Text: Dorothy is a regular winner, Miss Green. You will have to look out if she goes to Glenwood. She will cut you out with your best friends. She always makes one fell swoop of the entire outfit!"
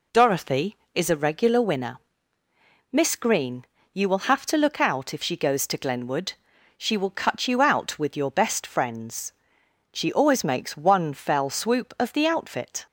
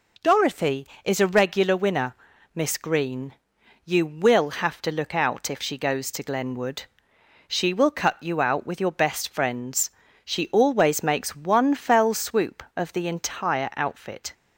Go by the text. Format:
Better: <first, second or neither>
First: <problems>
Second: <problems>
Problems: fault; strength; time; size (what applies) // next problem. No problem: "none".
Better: second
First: skips "entire"; at 12.2 s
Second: none